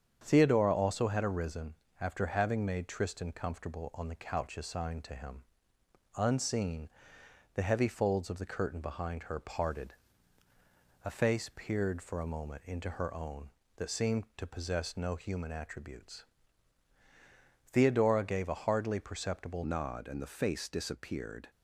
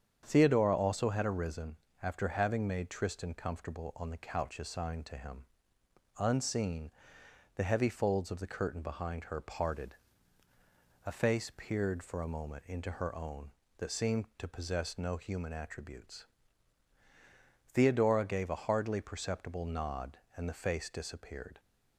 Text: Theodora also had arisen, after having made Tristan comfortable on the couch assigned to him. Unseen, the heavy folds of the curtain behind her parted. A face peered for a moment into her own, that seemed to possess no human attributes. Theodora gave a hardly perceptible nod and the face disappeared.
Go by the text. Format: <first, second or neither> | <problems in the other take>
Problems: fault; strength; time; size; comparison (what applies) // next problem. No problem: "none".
second | starts louder than the rest; strong; until 1.2 s; 8 dB; strong in the second // changes voice at "nod"; from 19.6 s on; 1.8 s long